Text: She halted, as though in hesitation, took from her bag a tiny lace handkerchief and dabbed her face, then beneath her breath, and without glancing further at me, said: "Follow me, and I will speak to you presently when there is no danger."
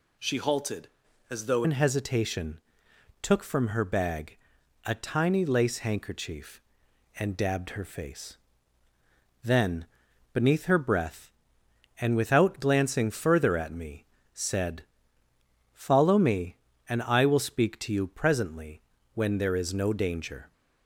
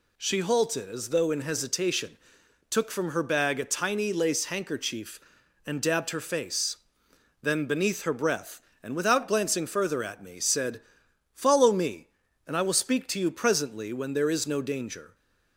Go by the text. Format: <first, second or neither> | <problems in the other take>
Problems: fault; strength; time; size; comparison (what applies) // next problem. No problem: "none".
second | changes voice at "in"; from 1.6 s on; 18.9 s long // pauses between "bag" and "a"; noticeable; at 4.3 s; 0.50 s long // pauses between "then" and "beneath"; noticeable; at 9.8 s; 0.48 s long // pauses between "presently" and "when"; slight; at 18.8 s; 0.32 s long